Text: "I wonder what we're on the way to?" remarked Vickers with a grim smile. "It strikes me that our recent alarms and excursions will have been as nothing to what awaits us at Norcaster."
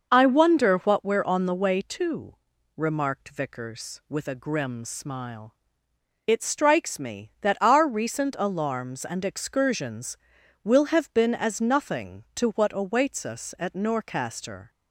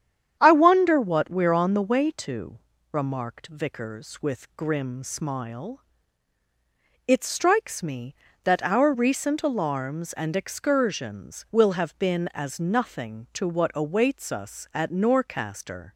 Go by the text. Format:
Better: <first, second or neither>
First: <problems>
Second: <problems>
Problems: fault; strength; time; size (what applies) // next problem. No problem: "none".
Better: first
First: none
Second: starts louder than the rest; strong; until 1.4 s; 9 dB // skips "a"; at 4.5 s